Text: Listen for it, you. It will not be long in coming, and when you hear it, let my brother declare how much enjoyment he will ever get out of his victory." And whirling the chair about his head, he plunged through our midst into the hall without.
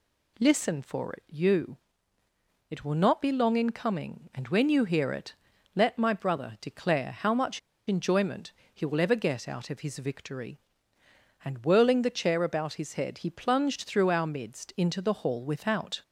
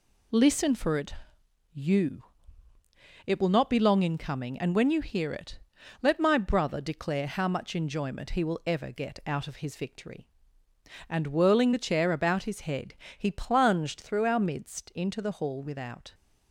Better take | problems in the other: second | pauses between "much" and "enjoyment"; slight; at 7.5 s; 0.28 s long // pauses between "enjoyment" and "he"; slight; at 8.5 s; 0.20 s long

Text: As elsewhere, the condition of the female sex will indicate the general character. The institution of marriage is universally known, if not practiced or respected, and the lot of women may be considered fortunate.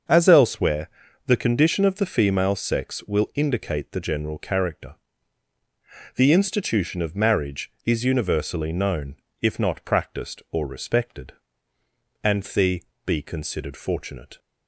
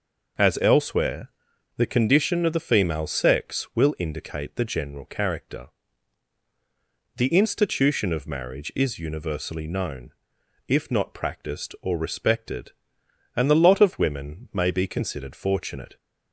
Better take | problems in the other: second | starts louder than the rest; until 1.4 s; 6.5 dB // skips "lot of women may"; at 12.9 s

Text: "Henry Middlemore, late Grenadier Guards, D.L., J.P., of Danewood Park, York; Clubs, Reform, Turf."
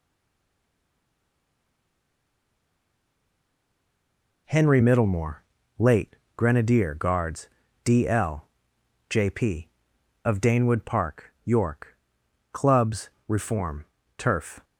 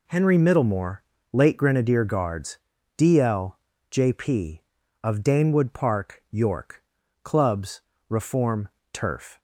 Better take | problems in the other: second | stays silent before the first word; strong; until 4.4 s; 4.4 s long // pauses between "late" and "Grenadier"; slight; at 6.1 s; 0.20 s long

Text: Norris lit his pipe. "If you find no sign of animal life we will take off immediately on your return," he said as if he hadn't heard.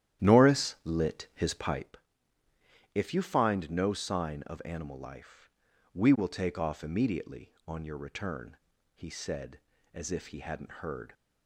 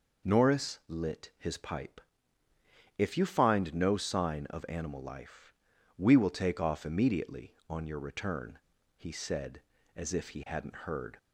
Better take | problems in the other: second | starts louder than the rest; strong; until 1.9 s; 11.5 dB // pauses between "life" and "we"; at 5.4 s; 0.44 s long; also in the second

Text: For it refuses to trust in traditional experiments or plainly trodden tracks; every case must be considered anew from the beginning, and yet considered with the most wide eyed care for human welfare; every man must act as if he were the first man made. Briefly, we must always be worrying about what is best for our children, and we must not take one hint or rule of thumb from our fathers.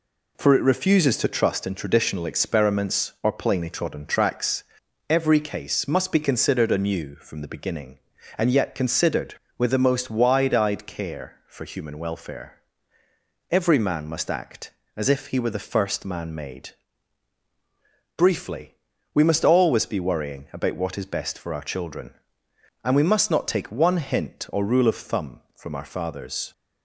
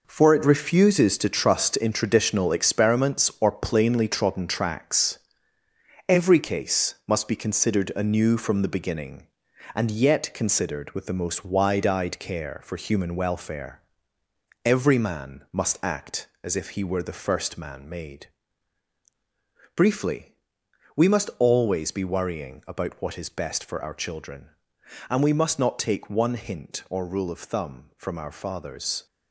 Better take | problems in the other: first | gets quieter; strong; throughout; 9.5 dB

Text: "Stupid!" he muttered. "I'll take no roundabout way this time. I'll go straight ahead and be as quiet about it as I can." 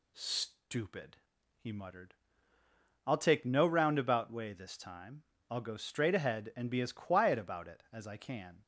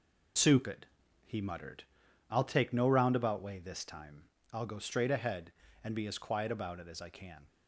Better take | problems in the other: neither | none

